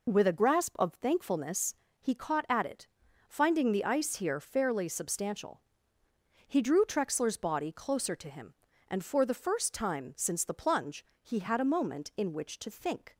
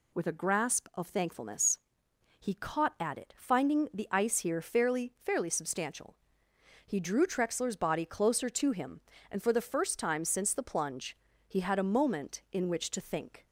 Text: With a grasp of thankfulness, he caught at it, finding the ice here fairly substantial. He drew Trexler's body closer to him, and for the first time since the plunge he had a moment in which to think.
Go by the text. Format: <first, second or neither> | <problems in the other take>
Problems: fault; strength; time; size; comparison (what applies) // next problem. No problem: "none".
first | says "fairly" twice; at 5.2 s // pauses between "plunge" and "he"; slight; at 11.1 s; 0.30 s long; slight in the first